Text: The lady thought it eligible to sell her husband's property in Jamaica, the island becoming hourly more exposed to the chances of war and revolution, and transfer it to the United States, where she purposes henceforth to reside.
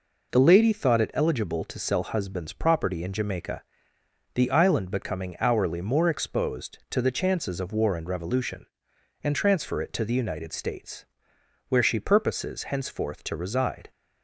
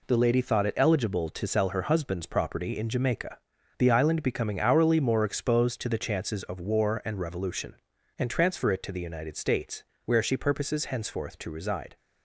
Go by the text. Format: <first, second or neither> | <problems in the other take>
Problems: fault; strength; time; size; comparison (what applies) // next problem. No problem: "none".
second | skips "her"; at 2.0 s